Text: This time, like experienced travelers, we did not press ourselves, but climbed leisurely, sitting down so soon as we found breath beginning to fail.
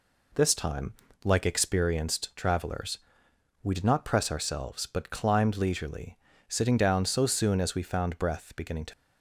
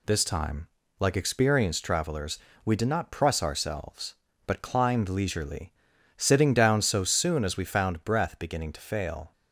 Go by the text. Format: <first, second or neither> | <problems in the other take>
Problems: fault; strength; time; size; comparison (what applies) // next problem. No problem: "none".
second | stops before "fail"; at 8.9 s